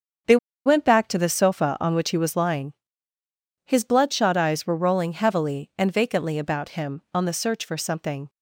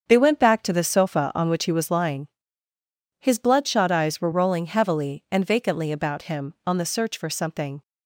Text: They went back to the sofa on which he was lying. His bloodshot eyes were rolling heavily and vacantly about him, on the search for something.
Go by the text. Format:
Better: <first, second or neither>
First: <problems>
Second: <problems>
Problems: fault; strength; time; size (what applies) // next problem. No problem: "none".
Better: second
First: starts louder than the rest; strong; until 1.5 s; 7.5 dB // pauses between "They" and "went"; slight; at 0.3 s; 0.29 s long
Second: starts louder than the rest; strong; until 1.1 s; 7.5 dB